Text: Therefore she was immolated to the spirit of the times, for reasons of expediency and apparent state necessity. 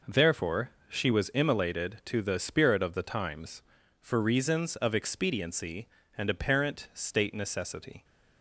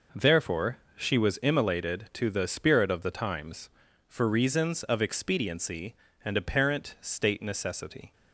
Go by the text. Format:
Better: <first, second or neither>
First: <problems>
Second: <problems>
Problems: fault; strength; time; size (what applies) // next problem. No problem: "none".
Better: neither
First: pauses between "Therefore" and "she"; slight; at 0.6 s; 0.18 s long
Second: pauses between "Therefore" and "she"; slight; at 0.7 s; 0.18 s long